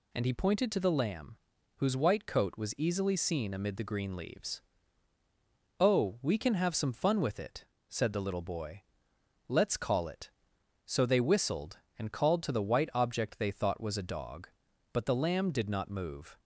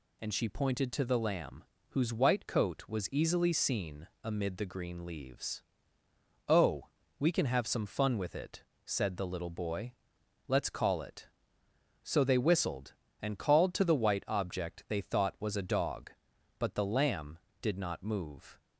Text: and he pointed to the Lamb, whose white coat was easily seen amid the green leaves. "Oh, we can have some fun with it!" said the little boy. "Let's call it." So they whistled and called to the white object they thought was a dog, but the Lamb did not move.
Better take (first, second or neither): first